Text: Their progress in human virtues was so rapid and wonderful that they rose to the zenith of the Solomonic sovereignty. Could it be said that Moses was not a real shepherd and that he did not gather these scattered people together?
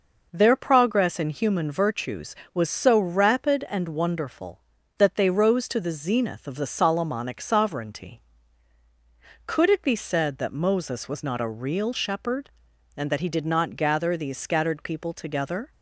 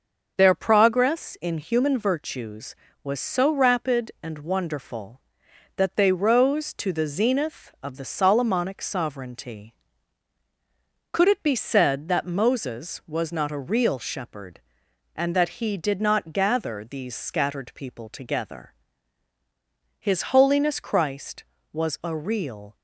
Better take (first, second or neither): first